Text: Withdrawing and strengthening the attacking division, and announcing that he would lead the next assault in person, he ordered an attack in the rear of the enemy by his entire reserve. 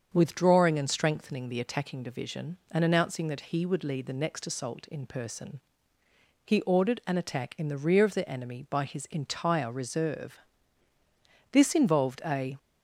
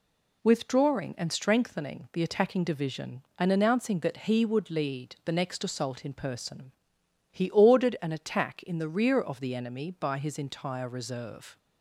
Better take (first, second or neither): second